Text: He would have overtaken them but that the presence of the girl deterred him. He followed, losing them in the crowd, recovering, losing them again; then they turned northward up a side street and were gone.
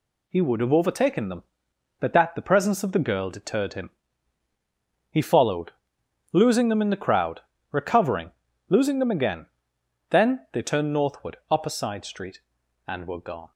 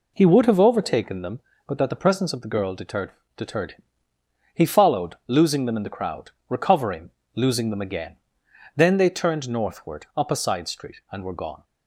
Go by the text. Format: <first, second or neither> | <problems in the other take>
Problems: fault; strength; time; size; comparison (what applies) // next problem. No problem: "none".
first | says "deterred" twice; at 3.3 s